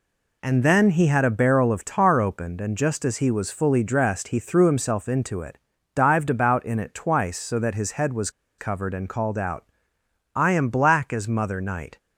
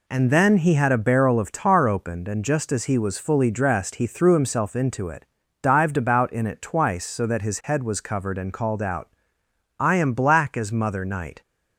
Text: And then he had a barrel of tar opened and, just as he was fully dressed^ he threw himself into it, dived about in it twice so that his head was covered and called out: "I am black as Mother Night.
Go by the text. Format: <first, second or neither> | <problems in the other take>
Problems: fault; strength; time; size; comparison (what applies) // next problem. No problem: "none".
second | pauses between "was" and "covered"; slight; at 8.2 s; 0.29 s long